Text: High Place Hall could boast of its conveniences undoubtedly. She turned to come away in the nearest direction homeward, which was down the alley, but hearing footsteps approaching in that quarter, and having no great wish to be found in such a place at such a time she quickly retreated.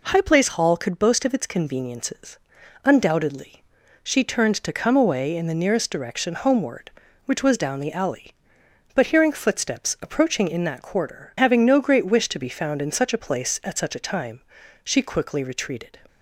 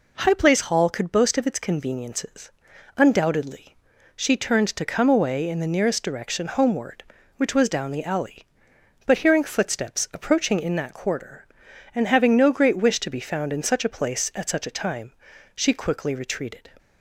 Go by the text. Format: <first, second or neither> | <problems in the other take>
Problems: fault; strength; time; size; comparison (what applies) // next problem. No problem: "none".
second | pauses between "conveniences" and "undoubtedly"; noticeable; at 2.3 s; 0.46 s long; noticeable in the second // skips "and"; at 11.3 s // pauses between "time" and "she"; at 14.4 s; 0.44 s long; also in the second